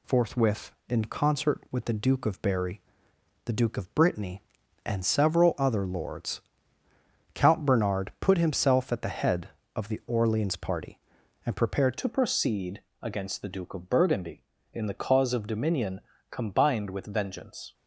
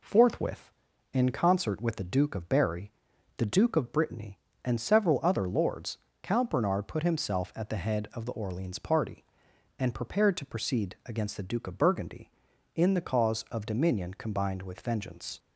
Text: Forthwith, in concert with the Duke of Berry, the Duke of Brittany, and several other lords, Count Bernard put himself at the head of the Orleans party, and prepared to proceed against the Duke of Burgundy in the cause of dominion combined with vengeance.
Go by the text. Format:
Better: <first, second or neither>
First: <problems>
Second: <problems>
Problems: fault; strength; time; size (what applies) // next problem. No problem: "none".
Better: second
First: changes voice at "to"; from 11.9 s on; 5.8 s long // pauses between "proceed" and "against"; slight; at 12.8 s; 0.22 s long // pauses between "dominion" and "combined"; slight; at 16.0 s; 0.30 s long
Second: none